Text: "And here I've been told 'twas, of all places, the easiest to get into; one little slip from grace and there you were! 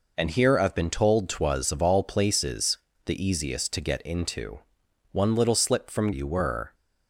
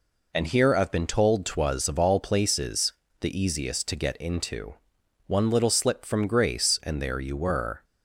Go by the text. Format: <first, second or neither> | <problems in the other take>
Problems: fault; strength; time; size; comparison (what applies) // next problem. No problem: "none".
second | skips "grace and there"; at 6.1 s